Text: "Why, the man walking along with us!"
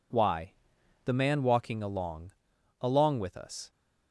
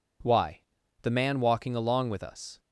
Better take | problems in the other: second | says "along" twice; at 2.8 s

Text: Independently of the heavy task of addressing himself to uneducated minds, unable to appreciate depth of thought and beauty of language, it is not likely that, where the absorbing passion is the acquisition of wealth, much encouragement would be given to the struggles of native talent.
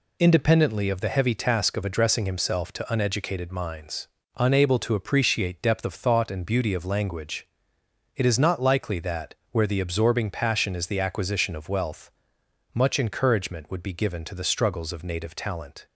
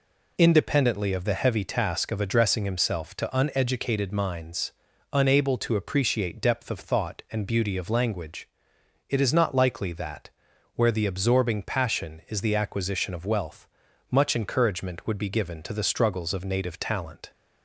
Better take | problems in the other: neither | none

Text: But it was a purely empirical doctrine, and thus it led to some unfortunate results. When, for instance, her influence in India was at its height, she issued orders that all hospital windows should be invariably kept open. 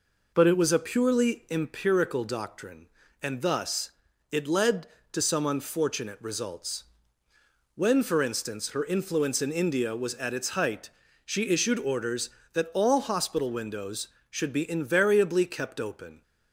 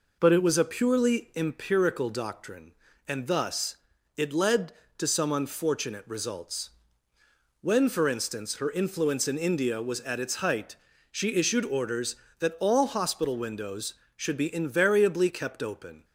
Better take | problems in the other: neither | pauses between "thus" and "it"; the same in both

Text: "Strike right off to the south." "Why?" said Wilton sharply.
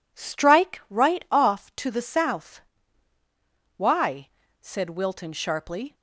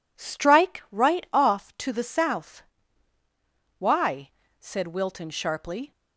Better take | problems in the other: neither | none

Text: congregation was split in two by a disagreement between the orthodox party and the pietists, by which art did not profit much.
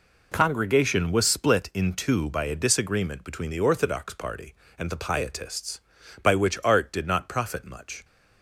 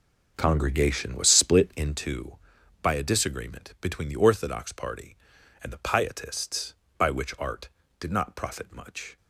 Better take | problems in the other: first | starts louder than the rest; noticeable; until 2.0 s; 5.5 dB

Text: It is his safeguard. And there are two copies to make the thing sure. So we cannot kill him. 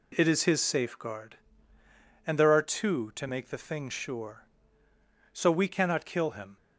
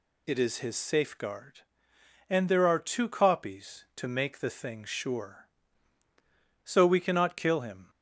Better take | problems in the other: second | skips "copies"; at 3.1 s

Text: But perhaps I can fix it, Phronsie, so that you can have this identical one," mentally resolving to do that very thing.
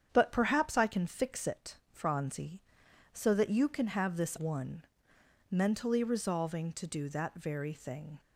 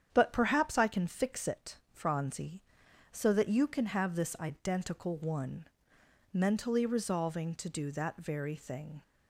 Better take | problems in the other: second | starts louder than the rest; strong; until 1.1 s; 8.5 dB; strong in the second // skips "identical"; at 4.3 s

